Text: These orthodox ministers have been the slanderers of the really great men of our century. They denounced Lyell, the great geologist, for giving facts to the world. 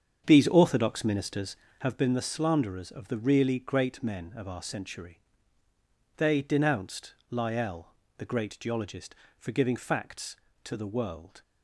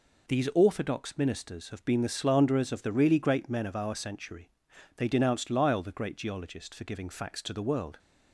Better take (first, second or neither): second